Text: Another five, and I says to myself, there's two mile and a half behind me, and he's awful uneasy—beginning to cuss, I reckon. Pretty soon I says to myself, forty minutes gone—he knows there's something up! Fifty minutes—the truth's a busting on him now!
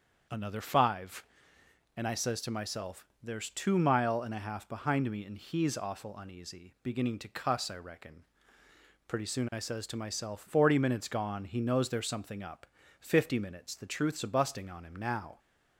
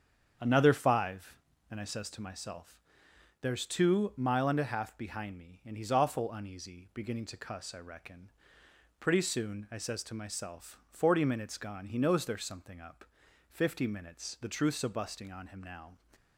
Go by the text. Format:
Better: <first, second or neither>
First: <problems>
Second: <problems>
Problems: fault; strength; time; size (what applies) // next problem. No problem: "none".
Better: neither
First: starts louder than the rest; strong; until 2.0 s; 7.5 dB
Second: starts louder than the rest; strong; until 1.7 s; 7.5 dB